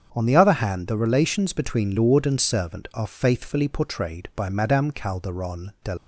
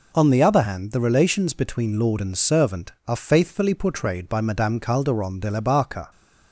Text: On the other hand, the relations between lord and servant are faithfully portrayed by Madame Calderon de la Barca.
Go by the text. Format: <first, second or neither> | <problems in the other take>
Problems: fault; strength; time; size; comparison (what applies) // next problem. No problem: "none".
second | starts louder than the rest; strong; until 1.1 s; 7 dB // stops before "la Barca"; at 5.9 s